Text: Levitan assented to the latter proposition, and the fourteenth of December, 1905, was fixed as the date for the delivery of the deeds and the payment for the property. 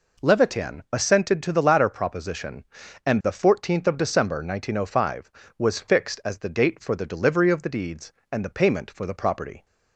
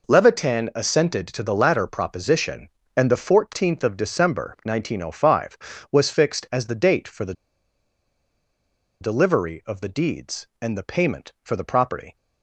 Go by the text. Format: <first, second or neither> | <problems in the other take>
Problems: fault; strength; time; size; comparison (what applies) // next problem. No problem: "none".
first | pauses between "the" and "delivery"; strong; at 7.3 s; 1.6 s long